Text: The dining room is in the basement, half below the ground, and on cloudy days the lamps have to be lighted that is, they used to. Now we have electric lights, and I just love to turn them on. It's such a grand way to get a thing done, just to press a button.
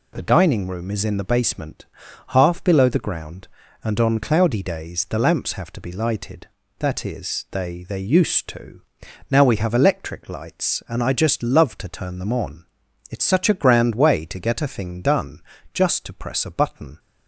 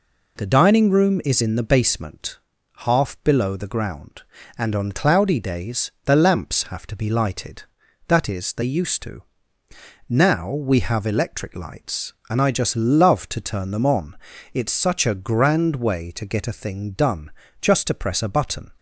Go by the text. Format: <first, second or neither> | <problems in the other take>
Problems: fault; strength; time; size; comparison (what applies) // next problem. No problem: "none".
second | says "they" twice; at 7.8 s